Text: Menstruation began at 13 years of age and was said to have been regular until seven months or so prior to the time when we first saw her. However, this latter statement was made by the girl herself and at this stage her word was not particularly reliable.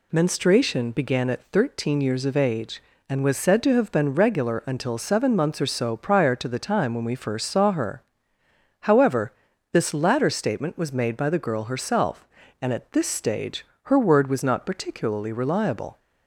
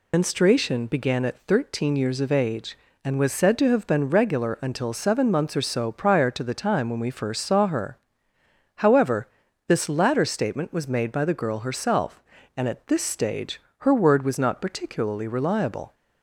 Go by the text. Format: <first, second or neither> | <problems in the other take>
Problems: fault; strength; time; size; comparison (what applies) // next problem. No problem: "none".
first | loses the start of "Menstruation"; at 0.1 s; 70 ms // pauses between "stage" and "her"; slight; at 13.5 s; 0.20 s long; slight in the first